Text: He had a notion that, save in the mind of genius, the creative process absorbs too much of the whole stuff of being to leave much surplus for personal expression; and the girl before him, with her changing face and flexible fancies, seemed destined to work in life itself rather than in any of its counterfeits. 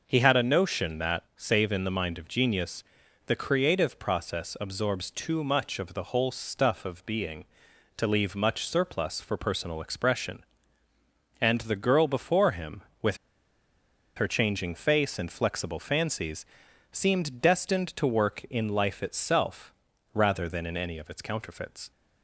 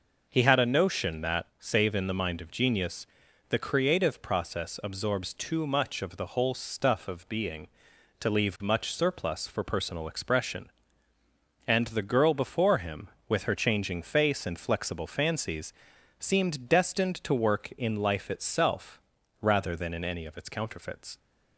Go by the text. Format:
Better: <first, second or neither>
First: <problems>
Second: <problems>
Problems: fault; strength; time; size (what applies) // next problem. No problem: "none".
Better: second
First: pauses between "with" and "her"; at 13.1 s; 1.0 s long // pauses between "itself" and "rather"; at 19.7 s; 0.40 s long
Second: pauses between "itself" and "rather"; at 19.0 s; 0.40 s long